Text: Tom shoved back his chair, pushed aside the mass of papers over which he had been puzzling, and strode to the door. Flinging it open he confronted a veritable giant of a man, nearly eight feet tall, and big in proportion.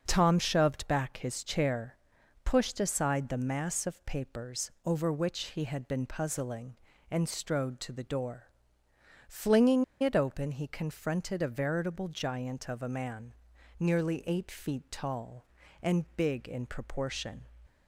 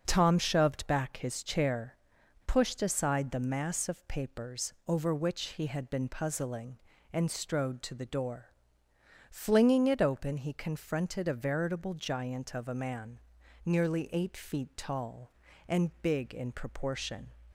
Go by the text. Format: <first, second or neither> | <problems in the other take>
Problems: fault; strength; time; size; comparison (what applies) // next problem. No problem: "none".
second | starts louder than the rest; until 1.0 s; 6.5 dB; also in the second // pauses between "Flinging" and "it"; slight; at 9.8 s; 0.16 s long